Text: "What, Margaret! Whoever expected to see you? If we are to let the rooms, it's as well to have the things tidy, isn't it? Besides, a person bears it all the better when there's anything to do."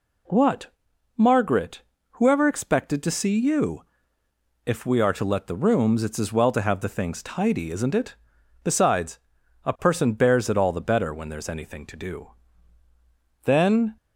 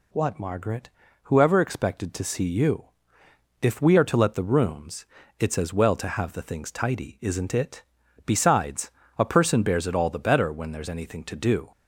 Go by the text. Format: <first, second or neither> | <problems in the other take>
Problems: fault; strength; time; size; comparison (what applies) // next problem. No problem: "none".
second | goes on to say "Then"; from 13.4 s on; 0.50 s long